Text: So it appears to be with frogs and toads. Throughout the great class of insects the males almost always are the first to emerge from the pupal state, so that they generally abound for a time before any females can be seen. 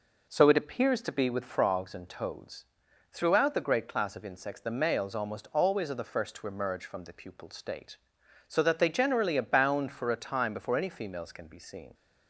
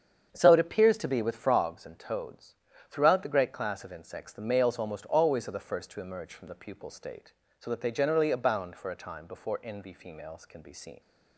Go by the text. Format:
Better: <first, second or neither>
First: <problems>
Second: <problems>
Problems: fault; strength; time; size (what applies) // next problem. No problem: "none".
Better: first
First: none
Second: starts louder than the rest; strong; until 1.3 s; 7.5 dB // says "envy" for "any"; at 9.6 s